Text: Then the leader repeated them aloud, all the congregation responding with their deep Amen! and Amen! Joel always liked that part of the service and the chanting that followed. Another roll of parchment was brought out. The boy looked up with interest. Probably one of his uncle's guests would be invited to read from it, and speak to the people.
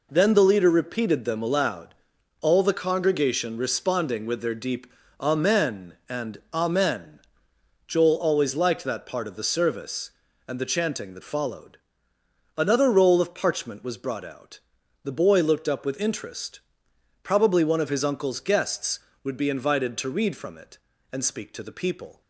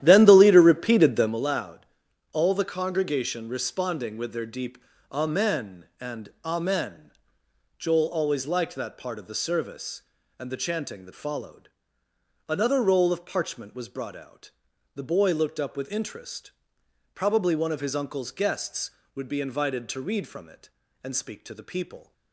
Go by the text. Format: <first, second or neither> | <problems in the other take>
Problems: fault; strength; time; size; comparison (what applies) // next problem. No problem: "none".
first | starts louder than the rest; strong; until 1.4 s; 11.5 dB // pauses between "deep" and "Amen"; slight; at 4.7 s; 0.32 s long; slight in the first // pauses between "and" and "Amen"; slight; at 6.2 s; 0.16 s long; slight in the first